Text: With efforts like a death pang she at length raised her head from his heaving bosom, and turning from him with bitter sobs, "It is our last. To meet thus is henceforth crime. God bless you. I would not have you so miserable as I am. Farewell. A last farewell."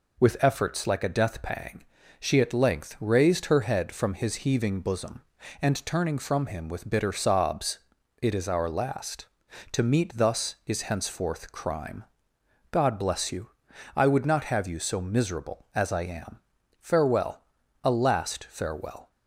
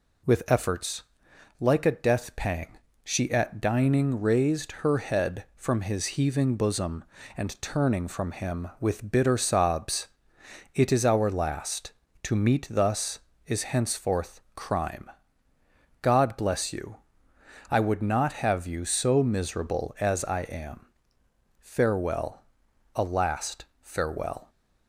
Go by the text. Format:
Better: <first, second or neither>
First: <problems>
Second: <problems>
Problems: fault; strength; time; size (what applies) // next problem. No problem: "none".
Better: first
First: pauses between "pang" and "she"; slight; at 1.8 s; 0.36 s long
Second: pauses between "efforts" and "like"; noticeable; at 1.0 s; 0.58 s long // pauses between "pang" and "she"; slight; at 2.7 s; 0.26 s long // says "dining" for "length"; at 3.6 s // pauses between "henceforth" and "crime"; slight; at 14.3 s; 0.16 s long // pauses between "last" and "farewell"; slight; at 23.6 s; 0.16 s long